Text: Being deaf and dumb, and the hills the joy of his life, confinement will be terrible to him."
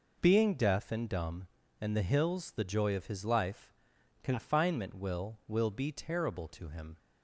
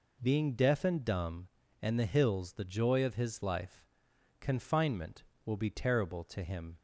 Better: second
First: says "will" twice; at 5.4 s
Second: none

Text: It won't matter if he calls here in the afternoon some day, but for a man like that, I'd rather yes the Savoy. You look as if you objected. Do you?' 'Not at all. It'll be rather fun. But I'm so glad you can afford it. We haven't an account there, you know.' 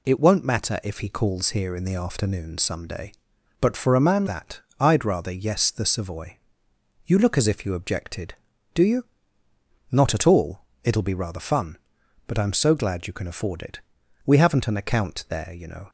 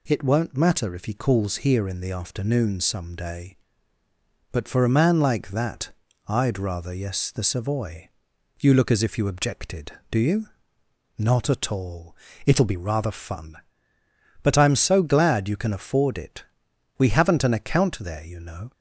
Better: second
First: skips "like"; at 4.2 s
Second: none

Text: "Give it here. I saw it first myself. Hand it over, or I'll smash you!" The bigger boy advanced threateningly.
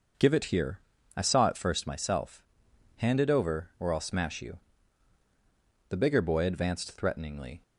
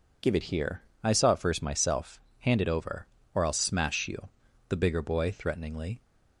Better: first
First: none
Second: skips "advanced"; at 5.3 s

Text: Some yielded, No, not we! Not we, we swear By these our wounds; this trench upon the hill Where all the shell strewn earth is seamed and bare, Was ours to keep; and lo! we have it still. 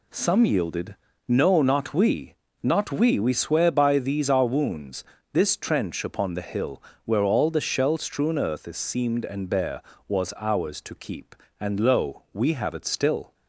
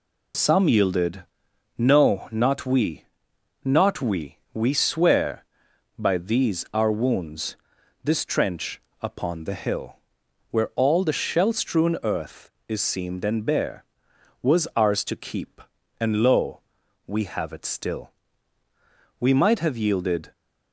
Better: first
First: pauses between "hill" and "Where"; slight; at 6.8 s; 0.24 s long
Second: pauses between "trench" and "upon"; slight; at 8.8 s; 0.18 s long // pauses between "hill" and "Where"; noticeable; at 9.9 s; 0.54 s long // goes on to say "We might have yielded"; noticeable; from 19.1 s on; 1.1 s long

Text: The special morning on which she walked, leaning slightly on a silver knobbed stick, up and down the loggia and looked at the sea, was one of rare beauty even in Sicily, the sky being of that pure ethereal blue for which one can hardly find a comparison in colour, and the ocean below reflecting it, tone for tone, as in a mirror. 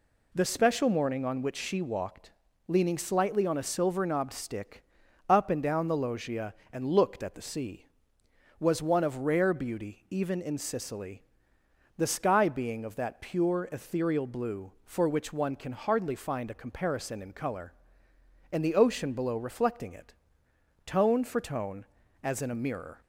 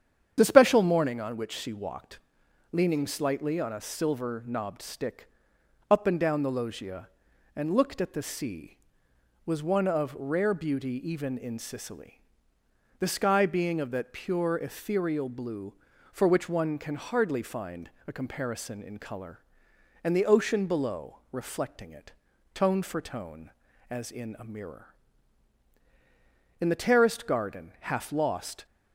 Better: first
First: none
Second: starts louder than the rest; strong; until 1.3 s; 8.5 dB // pauses between "find" and "a"; slight; at 17.9 s; 0.16 s long // goes on to say "In the terraced garden half lost"; strong; from 26.5 s on; 2.0 s long

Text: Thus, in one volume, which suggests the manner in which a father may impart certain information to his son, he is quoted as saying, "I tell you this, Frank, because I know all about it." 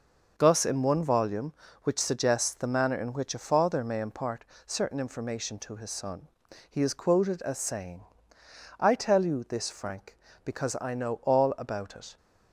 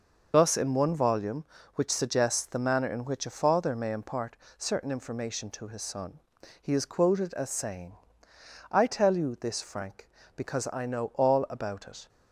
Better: first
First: pauses between "impart" and "certain"; slight; at 4.4 s; 0.22 s long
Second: loses the start of "Thus"; at 0.3 s; 40 ms // pauses between "impart" and "certain"; slight; at 4.3 s; 0.22 s long

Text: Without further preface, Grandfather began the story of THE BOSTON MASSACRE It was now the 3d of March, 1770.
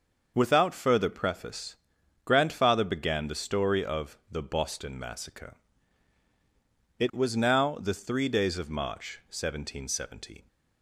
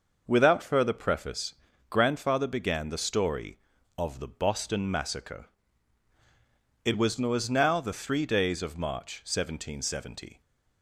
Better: first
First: starts louder than the rest; until 1.3 s; 6 dB // pauses between "MASSACRE" and "It"; strong; at 5.5 s; 1.4 s long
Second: starts louder than the rest; noticeable; until 1.2 s; 6 dB // pauses between "MASSACRE" and "It"; strong; at 5.4 s; 1.3 s long // says "was" twice; at 7.1 s

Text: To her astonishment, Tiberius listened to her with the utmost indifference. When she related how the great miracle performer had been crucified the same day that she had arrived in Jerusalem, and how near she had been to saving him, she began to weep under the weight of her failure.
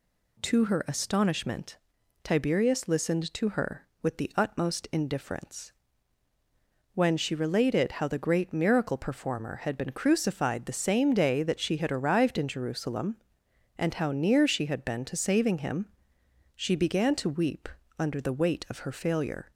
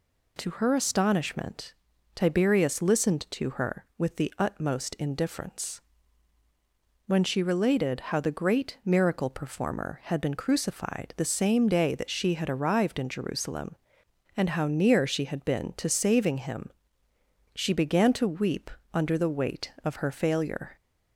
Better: neither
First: pauses between "weep" and "under"; slight; at 17.6 s; 0.32 s long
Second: pauses between "weep" and "under"; slight; at 18.6 s; 0.24 s long

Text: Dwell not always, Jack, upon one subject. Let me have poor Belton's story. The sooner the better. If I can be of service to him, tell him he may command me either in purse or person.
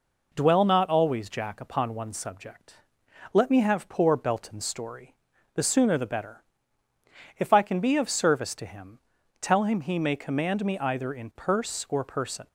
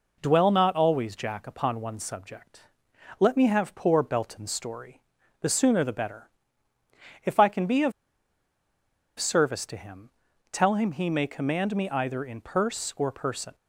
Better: first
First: none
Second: pauses between "of" and "service"; strong; at 7.9 s; 1.2 s long

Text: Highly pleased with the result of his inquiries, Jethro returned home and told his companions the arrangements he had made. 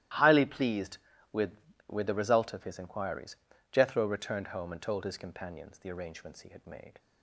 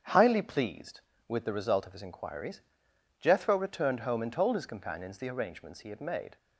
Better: second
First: starts louder than the rest; strong; until 1.5 s; 14 dB // says "with" twice; at 1.8 s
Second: starts louder than the rest; strong; until 1.3 s; 8 dB

